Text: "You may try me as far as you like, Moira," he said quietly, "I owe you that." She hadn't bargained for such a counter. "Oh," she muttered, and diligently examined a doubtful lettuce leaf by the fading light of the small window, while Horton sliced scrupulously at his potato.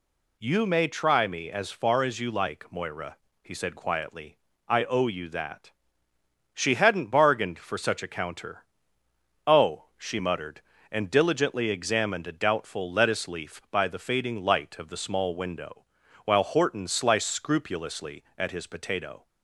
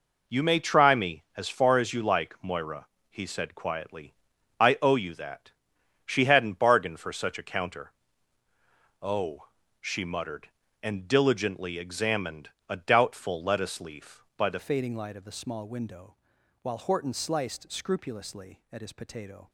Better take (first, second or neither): first